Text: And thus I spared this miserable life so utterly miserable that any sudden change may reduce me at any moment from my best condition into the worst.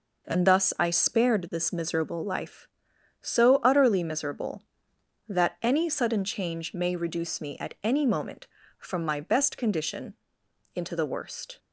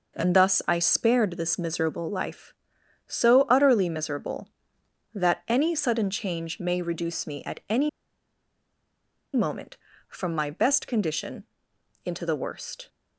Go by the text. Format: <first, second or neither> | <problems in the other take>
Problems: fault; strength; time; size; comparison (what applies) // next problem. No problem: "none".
first | pauses between "any" and "moment"; strong; at 7.8 s; 1.4 s long // pauses between "condition" and "into"; noticeable; at 11.4 s; 0.60 s long; noticeable in the first